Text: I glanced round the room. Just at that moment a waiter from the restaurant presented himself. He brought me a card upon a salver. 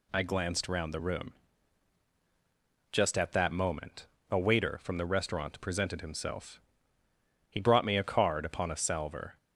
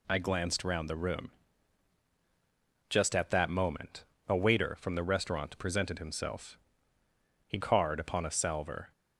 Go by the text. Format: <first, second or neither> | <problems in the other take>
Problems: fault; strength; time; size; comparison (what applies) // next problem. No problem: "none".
first | pauses between "moment" and "a"; slight; at 4.0 s; 0.22 s long; slight in the first // skips "brought me a"; at 7.5 s